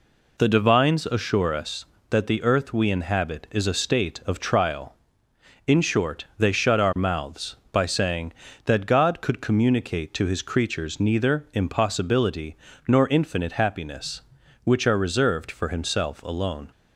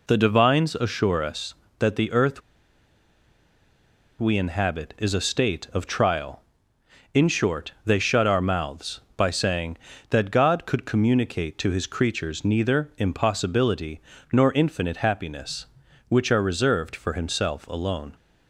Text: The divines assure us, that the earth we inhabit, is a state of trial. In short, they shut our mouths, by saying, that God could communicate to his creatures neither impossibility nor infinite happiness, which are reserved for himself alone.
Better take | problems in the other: first | pauses between "earth" and "we"; strong; at 2.3 s; 1.7 s long // pauses between "impossibility" and "nor"; slight; at 13.9 s; 0.32 s long; slight in the first

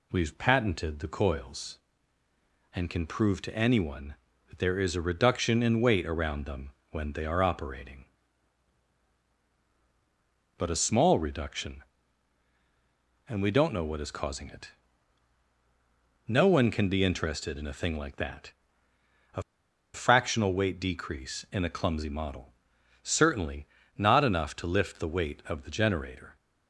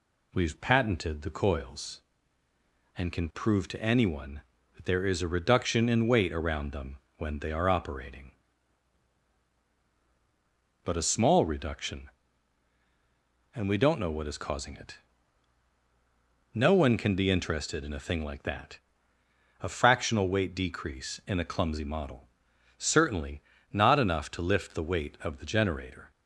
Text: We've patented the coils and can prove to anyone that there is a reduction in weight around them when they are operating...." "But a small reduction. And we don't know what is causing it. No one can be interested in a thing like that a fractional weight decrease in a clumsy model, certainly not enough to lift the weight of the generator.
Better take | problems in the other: second | pauses between "them" and "when"; slight; at 6.6 s; 0.22 s long; slight in the second // pauses between "that" and "a"; noticeable; at 18.5 s; 0.82 s long; noticeable in the second // pauses between "a" and "fractional"; noticeable; at 19.4 s; 0.52 s long // pauses between "certainly" and "not"; slight; at 23.6 s; 0.32 s long; slight in the second

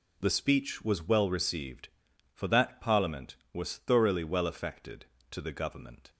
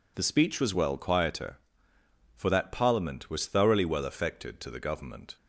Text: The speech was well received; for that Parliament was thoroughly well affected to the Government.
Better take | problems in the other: first | says "quieter" for "received"; at 0.9 s

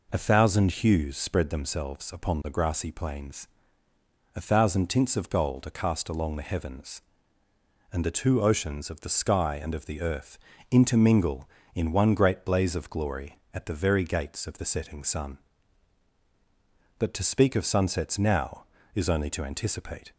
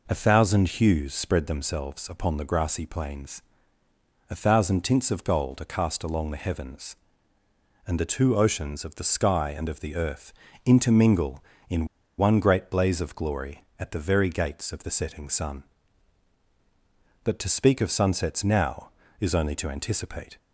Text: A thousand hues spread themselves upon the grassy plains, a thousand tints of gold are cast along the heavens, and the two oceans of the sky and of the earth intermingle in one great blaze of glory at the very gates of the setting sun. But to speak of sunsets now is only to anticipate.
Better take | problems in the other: first | pauses between "earth" and "intermingle"; slight; at 10.3 s; 0.32 s long; slight in the first // pauses between "in" and "one"; slight; at 11.8 s; 0.31 s long

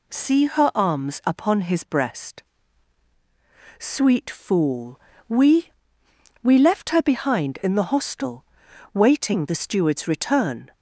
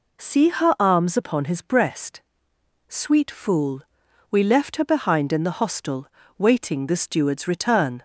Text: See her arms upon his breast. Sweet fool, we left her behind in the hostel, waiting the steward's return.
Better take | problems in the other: second | says "we" twice; at 6.4 s

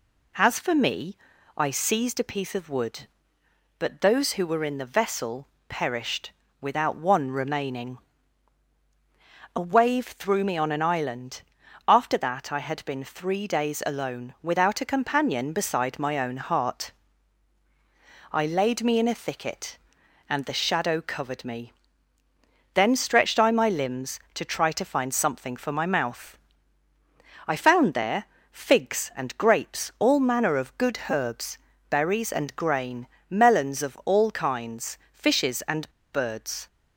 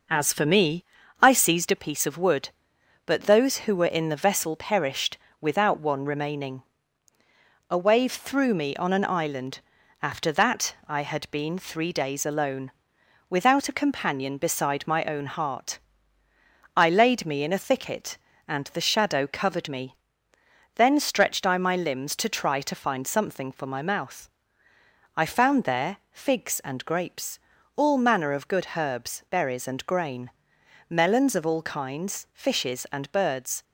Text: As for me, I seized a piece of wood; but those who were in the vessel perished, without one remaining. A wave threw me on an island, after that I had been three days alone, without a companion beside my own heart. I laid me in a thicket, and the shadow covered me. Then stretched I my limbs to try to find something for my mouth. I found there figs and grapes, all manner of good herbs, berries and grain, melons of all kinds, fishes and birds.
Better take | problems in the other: second | pauses between "vessel" and "perished"; slight; at 5.4 s; 0.22 s long // pauses between "there" and "figs"; slight; at 28.2 s; 0.26 s long // pauses between "and" and "birds"; slight; at 35.9 s; 0.21 s long

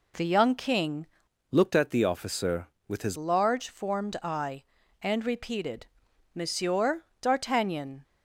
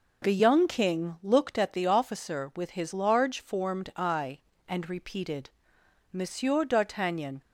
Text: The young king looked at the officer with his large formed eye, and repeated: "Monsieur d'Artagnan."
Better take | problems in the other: second | changes voice from "looked" to "his"; from 1.4 to 3.1 s; 1.7 s long // pauses between "Monsieur" and "d'Artagnan"; slight; at 7.0 s; 0.16 s long

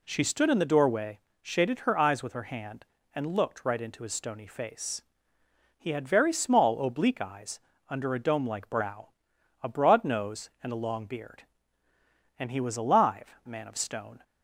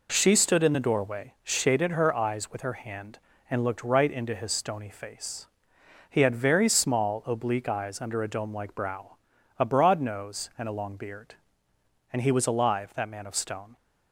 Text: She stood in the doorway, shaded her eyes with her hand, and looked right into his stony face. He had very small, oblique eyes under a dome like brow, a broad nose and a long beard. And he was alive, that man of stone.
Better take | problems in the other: second | pauses between "eyes" and "under"; slight; at 7.5 s; 0.28 s long // skips "that"; at 13.4 s

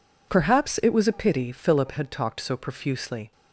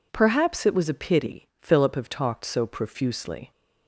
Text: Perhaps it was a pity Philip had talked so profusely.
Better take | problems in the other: first | says "have" for "had"; at 1.9 s

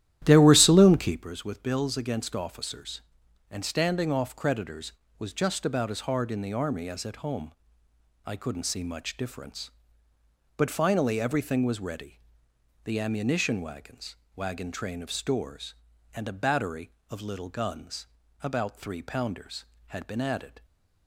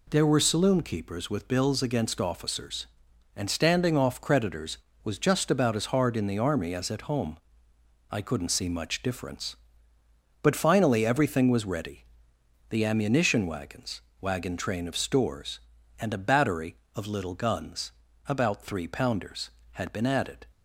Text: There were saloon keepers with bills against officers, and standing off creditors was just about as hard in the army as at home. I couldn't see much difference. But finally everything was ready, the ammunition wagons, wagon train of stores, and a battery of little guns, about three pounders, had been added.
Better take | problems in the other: second | starts louder than the rest; strong; until 1.3 s; 12 dB

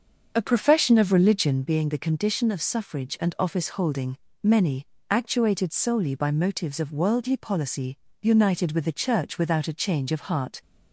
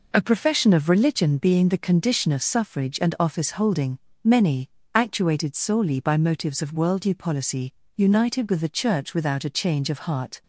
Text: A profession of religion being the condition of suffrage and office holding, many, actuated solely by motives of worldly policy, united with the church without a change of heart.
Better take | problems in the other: second | starts louder than the rest; until 1.7 s; 6.5 dB

